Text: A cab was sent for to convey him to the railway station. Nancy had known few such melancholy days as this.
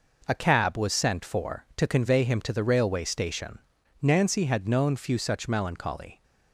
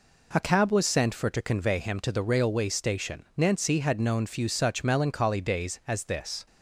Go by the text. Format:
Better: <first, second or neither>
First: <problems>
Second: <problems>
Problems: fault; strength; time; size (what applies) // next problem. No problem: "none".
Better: second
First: stops before "days as this"; at 6.2 s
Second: none